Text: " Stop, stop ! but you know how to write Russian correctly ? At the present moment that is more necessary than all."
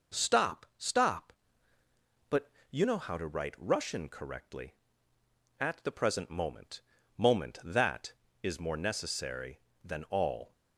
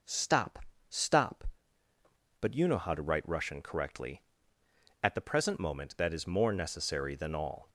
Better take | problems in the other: second | pauses between "but" and "you"; slight; at 2.5 s; 0.18 s long // says "moment" twice; at 7.1 s

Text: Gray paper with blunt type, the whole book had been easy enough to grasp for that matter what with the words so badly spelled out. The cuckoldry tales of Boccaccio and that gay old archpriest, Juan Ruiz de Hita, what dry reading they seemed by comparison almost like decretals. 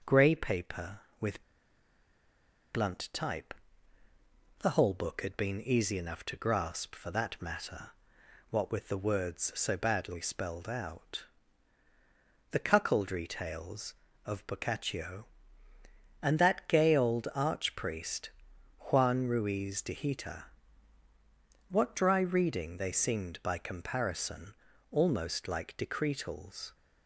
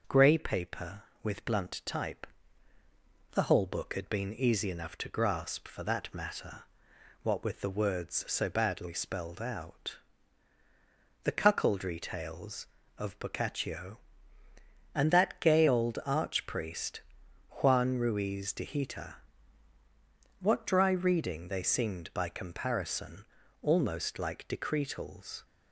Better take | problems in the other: second | pauses between "with" and "blunt"; strong; at 1.4 s; 1.3 s long // pauses between "matter" and "what"; noticeable; at 7.9 s; 0.58 s long; noticeable in the second // pauses between "comparison" and "almost"; slight; at 24.5 s; 0.36 s long; slight in the second

